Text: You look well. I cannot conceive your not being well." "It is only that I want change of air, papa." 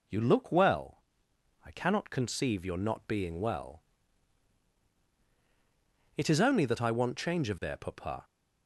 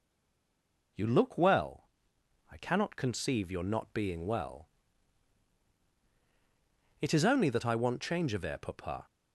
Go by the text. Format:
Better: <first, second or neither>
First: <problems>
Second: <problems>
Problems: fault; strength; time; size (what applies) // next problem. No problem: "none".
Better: first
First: none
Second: stays silent before the first word; slight; until 0.9 s; 0.9 s long